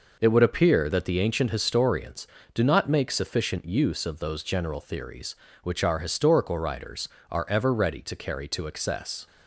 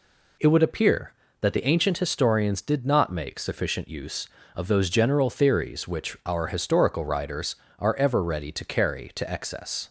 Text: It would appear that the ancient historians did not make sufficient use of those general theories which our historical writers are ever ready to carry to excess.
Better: second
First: says "do" for "did"; at 2.5 s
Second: none

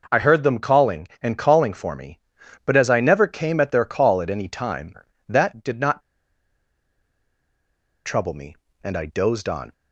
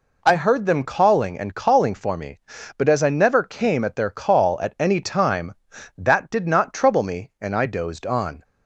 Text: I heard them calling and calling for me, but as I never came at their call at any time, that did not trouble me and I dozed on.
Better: second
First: pauses between "not" and "trouble"; strong; at 6.0 s; 2.0 s long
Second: none

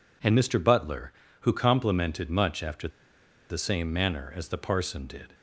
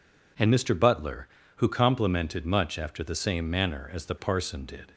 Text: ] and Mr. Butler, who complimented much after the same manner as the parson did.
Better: second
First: pauses between "after" and "the"; noticeable; at 2.8 s; 0.61 s long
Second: none

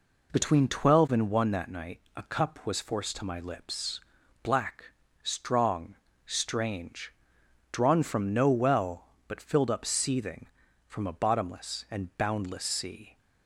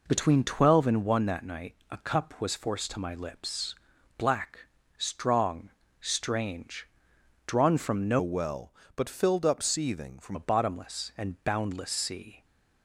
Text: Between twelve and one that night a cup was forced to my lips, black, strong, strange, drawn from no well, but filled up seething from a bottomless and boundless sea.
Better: first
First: pauses between "night" and "a"; slight; at 1.9 s; 0.16 s long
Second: pauses between "night" and "a"; slight; at 1.7 s; 0.16 s long // changes voice from "well" to "from"; from 8.2 to 10.3 s; 2.1 s long

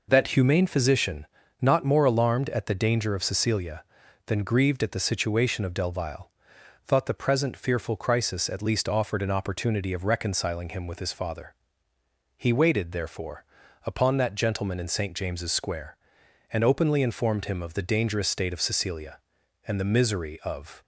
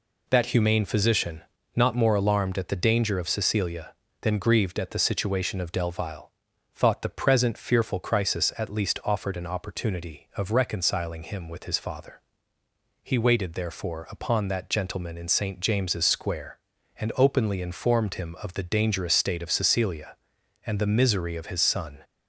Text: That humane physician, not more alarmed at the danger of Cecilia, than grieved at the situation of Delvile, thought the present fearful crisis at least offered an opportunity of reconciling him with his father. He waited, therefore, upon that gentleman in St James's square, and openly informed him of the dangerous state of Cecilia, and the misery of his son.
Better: second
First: stops before "his son"; at 20.8 s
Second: none

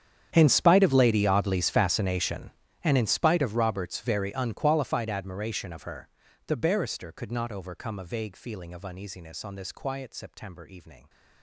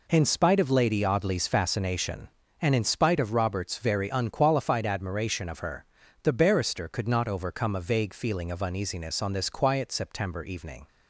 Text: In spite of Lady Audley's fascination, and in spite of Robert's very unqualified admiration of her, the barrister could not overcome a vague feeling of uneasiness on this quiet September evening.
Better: second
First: gets quieter; strong; throughout; 21 dB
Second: none

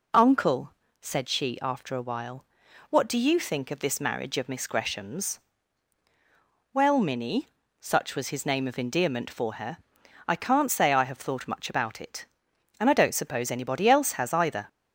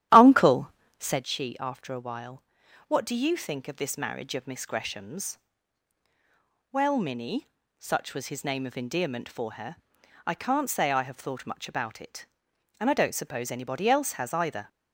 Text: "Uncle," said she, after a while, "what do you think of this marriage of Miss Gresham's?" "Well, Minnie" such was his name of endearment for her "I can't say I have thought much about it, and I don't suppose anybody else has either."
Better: first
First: pauses between "Minnie" and "such"; slight; at 7.4 s; 0.34 s long // pauses between "her" and "I"; noticeable; at 9.7 s; 0.46 s long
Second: starts louder than the rest; strong; until 1.2 s; 11.5 dB // pauses between "Minnie" and "such"; slight; at 7.4 s; 0.34 s long // pauses between "her" and "I"; noticeable; at 9.7 s; 0.46 s long

